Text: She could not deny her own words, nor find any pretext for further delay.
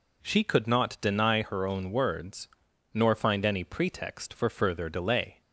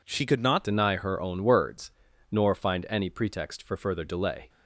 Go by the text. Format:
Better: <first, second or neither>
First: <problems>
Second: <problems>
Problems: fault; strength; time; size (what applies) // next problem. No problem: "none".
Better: first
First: none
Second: changes voice at "deny"; from 0.6 s on; 3.8 s long